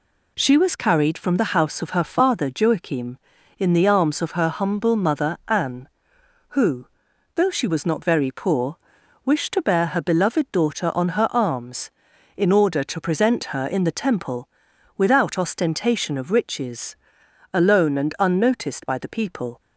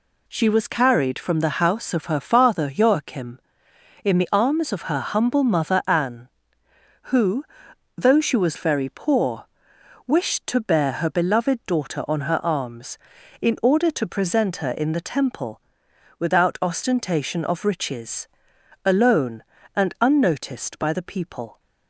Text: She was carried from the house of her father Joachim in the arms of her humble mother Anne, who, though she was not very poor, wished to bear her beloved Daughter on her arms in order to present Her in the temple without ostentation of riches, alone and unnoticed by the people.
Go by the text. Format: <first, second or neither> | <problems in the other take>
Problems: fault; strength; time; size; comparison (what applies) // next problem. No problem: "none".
first | skips "not"; at 8.5 s // pauses between "temple" and "without"; noticeable; at 15.6 s; 0.58 s long; noticeable in the first